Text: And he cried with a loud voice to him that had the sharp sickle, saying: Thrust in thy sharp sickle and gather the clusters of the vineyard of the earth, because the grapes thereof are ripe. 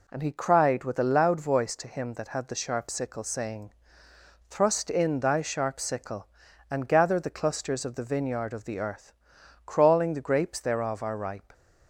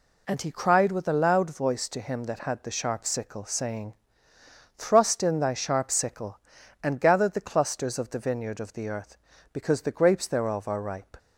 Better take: second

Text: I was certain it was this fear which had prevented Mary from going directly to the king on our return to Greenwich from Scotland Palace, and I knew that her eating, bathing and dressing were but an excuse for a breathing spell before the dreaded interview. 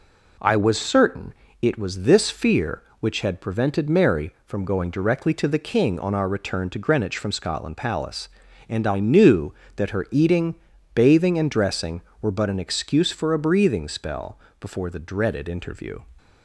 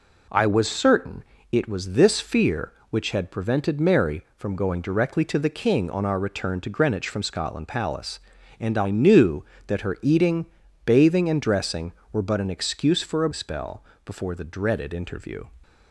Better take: first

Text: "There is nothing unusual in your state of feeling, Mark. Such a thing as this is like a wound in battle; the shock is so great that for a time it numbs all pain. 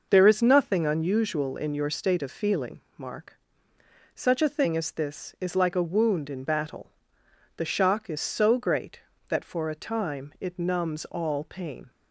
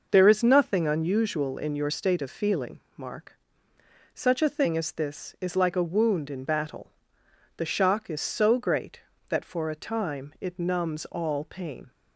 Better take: neither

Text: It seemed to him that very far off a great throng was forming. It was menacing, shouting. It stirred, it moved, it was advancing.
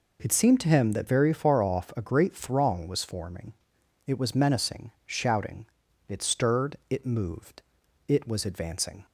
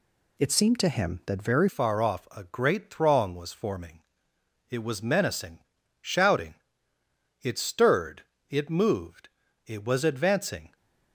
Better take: first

